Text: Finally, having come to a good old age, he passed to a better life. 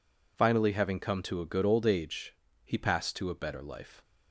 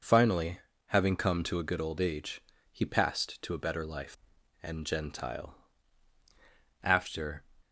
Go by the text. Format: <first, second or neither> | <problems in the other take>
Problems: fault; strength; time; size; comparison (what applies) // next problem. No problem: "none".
first | goes on to say "And Gentile after"; strong; from 4.6 s on; 2.8 s long